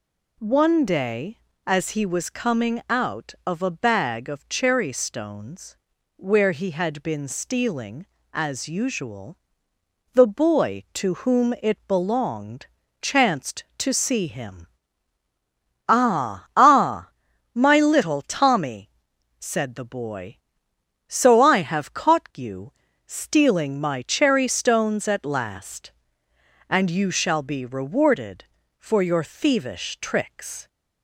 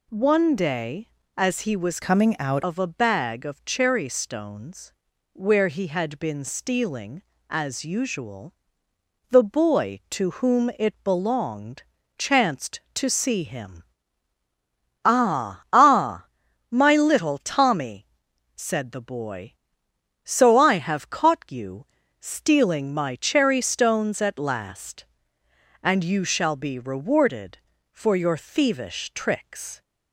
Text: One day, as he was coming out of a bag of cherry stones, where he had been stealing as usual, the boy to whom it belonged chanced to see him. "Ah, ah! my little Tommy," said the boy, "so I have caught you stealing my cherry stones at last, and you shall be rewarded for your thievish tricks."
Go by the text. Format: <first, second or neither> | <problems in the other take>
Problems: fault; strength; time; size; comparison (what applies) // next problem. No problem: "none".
first | changes voice from "coming" to "out"; from 2.0 to 2.6 s; 0.6 s long // pauses between "belonged" and "chanced"; slight; at 11.8 s; 0.34 s long; slight in the first // pauses between "you" and "stealing"; slight; at 21.8 s; 0.34 s long; slight in the first